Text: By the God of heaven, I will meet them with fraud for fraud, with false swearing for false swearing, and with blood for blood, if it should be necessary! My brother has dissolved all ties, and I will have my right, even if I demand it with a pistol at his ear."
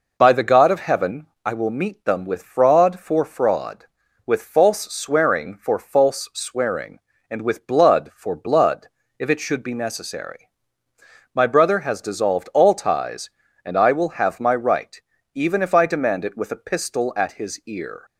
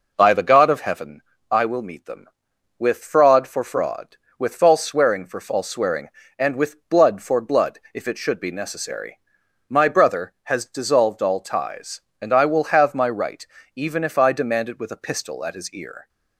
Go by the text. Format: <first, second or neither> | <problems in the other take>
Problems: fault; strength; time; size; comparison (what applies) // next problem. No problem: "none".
neither | none